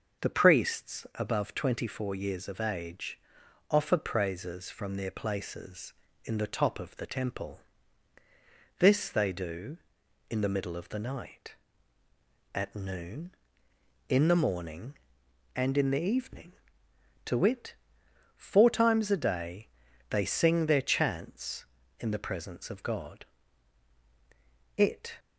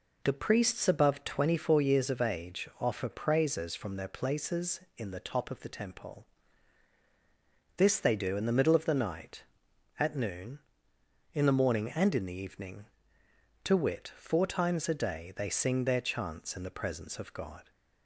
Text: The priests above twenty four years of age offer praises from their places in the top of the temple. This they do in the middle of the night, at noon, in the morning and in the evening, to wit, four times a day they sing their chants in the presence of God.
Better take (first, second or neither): second